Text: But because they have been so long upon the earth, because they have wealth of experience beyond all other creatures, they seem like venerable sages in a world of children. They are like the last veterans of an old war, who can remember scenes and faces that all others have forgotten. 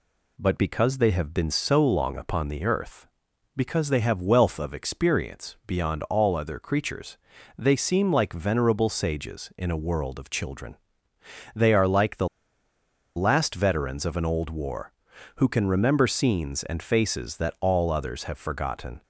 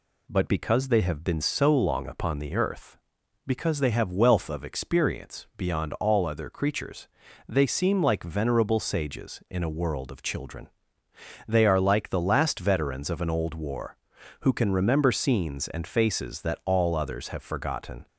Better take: second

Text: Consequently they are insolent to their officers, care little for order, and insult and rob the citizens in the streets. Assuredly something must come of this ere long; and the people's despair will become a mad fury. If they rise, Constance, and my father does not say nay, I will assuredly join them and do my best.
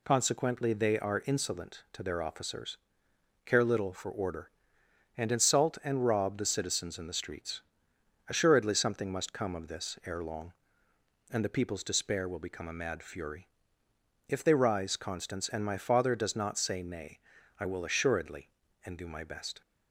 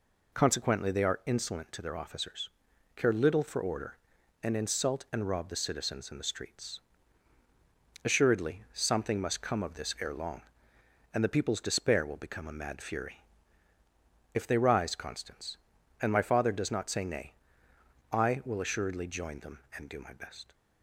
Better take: second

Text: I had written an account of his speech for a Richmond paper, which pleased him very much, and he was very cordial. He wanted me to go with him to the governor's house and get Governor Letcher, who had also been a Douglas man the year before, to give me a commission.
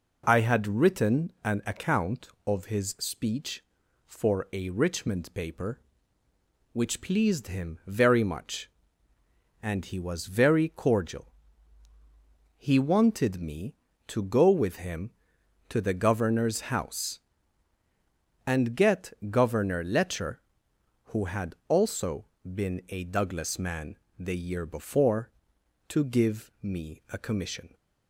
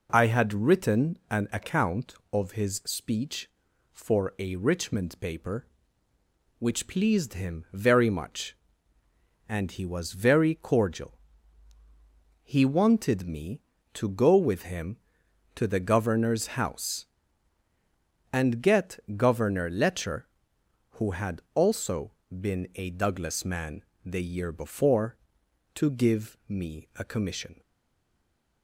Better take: first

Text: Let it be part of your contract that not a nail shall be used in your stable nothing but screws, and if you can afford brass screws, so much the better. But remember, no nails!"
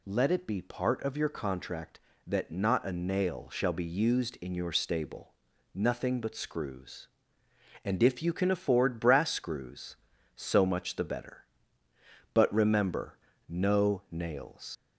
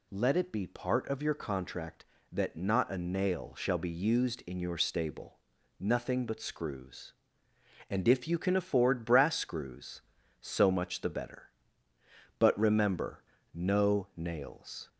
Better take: second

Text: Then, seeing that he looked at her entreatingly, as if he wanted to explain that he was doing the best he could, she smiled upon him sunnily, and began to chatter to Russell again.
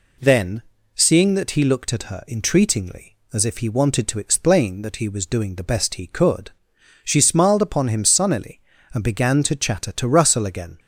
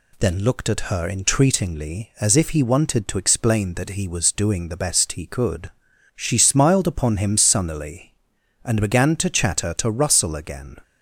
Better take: first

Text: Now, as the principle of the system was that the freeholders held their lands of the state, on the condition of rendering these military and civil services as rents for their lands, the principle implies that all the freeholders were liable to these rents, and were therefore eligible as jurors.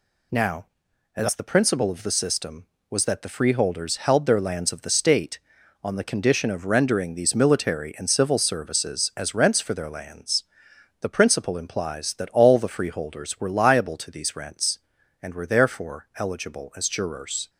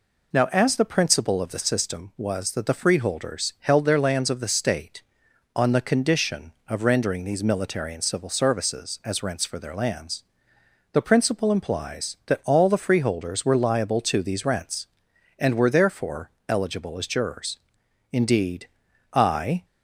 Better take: first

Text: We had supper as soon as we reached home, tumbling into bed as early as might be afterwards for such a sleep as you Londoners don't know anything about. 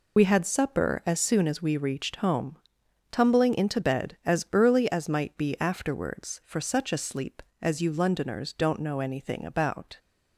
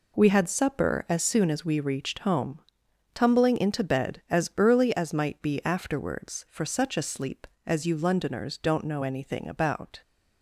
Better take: second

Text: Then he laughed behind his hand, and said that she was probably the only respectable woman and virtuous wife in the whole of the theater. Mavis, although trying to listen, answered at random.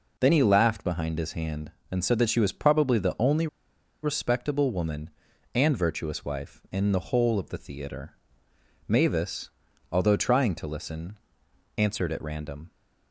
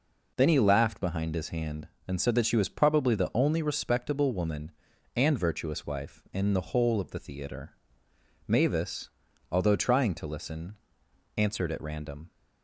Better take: second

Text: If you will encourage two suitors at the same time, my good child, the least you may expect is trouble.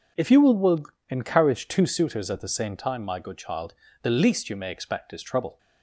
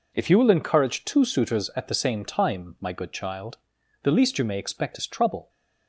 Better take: second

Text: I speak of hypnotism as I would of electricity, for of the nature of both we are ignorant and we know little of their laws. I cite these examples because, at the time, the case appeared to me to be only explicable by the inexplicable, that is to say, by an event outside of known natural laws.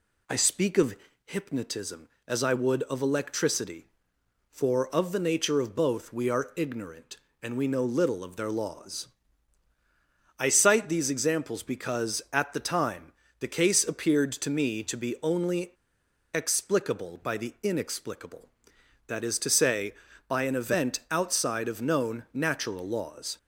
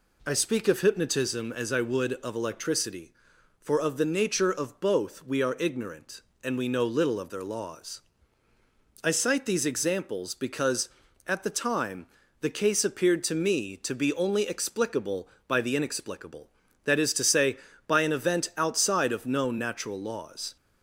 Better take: second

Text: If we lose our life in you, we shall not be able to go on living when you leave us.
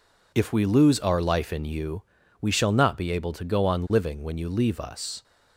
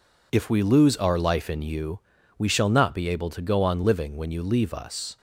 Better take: neither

